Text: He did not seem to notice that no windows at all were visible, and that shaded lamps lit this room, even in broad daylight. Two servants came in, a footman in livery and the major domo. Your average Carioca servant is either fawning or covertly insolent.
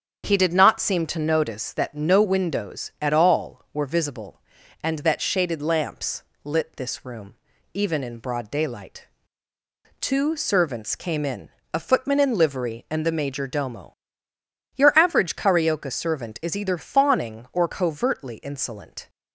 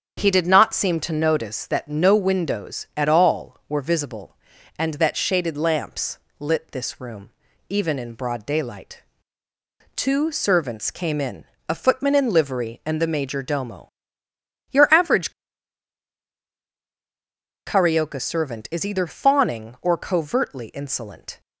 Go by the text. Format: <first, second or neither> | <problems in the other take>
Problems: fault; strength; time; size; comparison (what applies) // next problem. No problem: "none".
first | starts louder than the rest; strong; until 1.2 s; 8 dB; strong in the first // pauses between "lamps" and "lit"; slight; at 6.1 s; 0.22 s long; slight in the first // pauses between "average" and "Carioca"; strong; at 15.3 s; 2.3 s long